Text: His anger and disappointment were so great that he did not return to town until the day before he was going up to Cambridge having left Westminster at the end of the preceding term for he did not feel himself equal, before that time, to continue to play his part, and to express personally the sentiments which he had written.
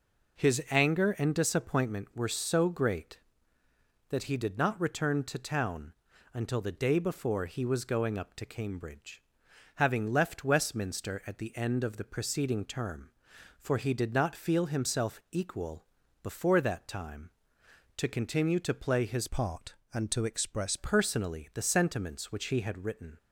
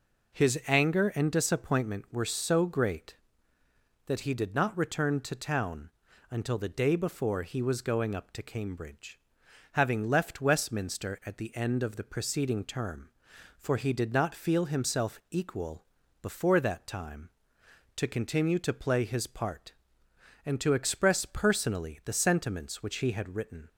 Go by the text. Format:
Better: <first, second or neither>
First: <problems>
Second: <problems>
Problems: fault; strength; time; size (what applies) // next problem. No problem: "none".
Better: second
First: pauses between "town" and "until"; at 5.9 s; 0.40 s long // pauses between "Cambridge" and "having"; noticeable; at 9.2 s; 0.54 s long // changes voice from "part" to "express"; from 19.2 to 20.7 s; 1.5 s long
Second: pauses between "town" and "until"; at 5.9 s; 0.40 s long // pauses between "Cambridge" and "having"; noticeable; at 9.1 s; 0.54 s long